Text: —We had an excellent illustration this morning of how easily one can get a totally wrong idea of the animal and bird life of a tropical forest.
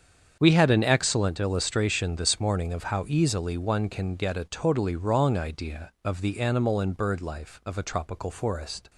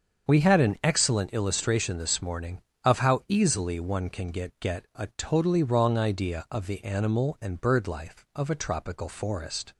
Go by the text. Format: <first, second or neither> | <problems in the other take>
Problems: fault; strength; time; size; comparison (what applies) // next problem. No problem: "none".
first | starts louder than the rest; until 1.3 s; 7 dB; strong in the first // says "get" twice; at 4.5 s